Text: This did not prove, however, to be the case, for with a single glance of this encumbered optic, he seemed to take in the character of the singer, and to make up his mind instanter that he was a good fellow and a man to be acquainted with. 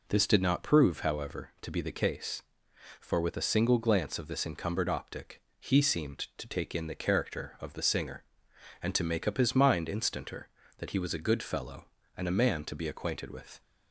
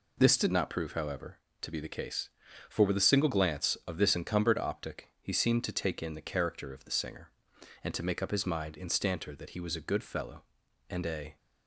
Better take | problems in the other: first | stops before "man to be acquainted with"; at 11.3 s

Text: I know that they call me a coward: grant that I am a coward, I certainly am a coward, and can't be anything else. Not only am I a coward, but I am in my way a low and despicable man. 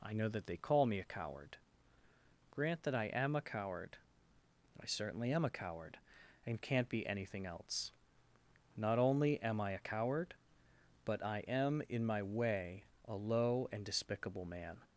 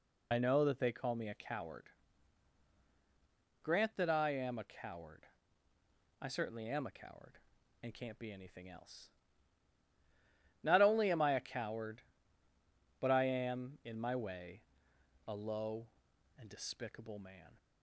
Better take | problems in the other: first | loses the start of "I"; at 0.3 s; 55 ms // pauses between "way" and "a"; noticeable; at 14.6 s; 0.66 s long; slight in the first

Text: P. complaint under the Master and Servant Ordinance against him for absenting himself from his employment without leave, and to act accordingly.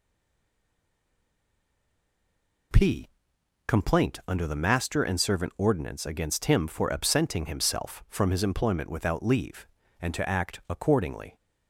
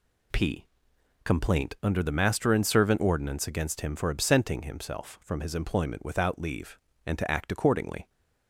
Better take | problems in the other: second | stays silent before the first word; strong; until 2.7 s; 2.7 s long

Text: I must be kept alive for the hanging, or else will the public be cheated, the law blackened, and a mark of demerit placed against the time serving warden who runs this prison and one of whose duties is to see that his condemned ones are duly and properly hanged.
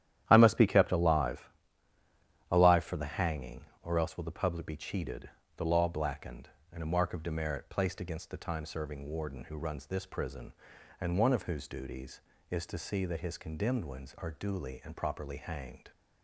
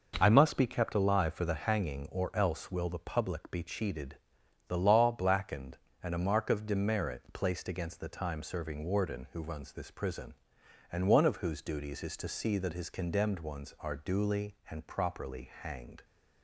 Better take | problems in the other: second | starts louder than the rest; strong; until 1.2 s; 11 dB // says "alive" twice; at 2.5 s

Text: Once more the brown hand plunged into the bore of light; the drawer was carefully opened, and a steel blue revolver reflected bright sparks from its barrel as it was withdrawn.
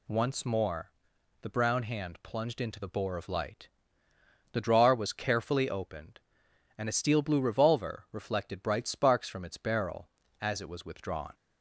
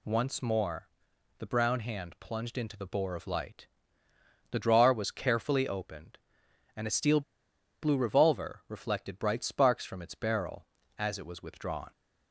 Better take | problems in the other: first | pauses between "more" and "the"; noticeable; at 0.8 s; 0.48 s long; noticeable in the first // pauses between "steel" and "blue"; noticeable; at 7.2 s; 0.61 s long

